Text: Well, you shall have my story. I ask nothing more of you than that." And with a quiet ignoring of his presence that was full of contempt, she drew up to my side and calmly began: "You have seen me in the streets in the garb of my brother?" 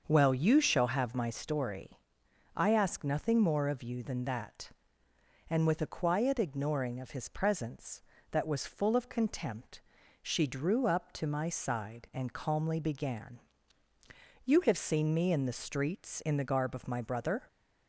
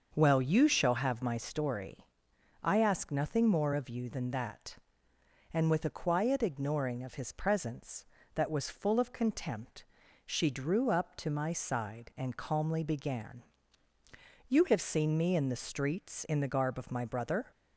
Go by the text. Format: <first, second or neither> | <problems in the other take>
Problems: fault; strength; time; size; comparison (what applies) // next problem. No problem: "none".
neither | starts louder than the rest; the same in both